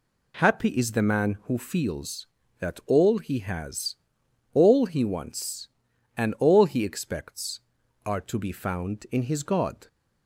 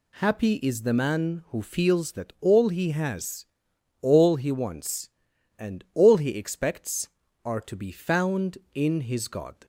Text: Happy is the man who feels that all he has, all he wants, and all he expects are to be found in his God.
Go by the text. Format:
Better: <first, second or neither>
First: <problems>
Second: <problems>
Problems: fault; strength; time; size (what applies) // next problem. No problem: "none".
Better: neither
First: none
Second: none